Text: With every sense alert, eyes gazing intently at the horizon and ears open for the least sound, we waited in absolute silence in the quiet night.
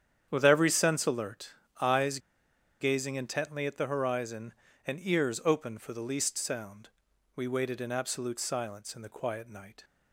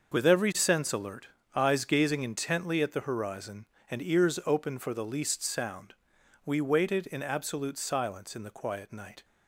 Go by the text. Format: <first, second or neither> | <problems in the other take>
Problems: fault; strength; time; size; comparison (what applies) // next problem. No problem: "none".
second | starts louder than the rest; strong; until 1.3 s; 9 dB; also in the second // pauses between "eyes" and "gazing"; noticeable; at 2.1 s; 0.62 s long